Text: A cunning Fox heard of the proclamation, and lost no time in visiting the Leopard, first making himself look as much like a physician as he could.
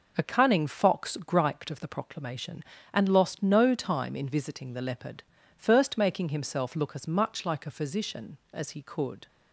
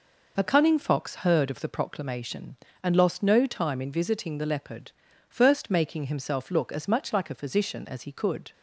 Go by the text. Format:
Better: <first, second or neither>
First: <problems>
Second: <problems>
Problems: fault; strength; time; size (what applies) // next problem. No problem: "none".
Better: second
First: says "griped" for "heard"; at 1.1 s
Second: none